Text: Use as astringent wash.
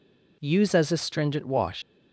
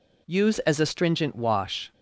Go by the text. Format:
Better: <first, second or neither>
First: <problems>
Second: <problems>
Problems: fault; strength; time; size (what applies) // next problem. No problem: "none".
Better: second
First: leaves "wash" unfinished; at 1.8 s; 80 ms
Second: none